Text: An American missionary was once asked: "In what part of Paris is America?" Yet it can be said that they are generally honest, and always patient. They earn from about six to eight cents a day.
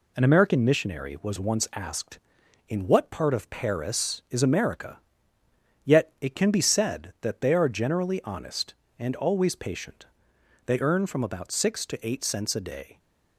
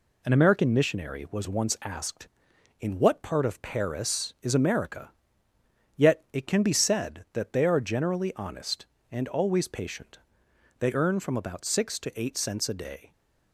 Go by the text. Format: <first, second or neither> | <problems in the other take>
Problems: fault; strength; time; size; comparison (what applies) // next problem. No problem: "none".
neither | none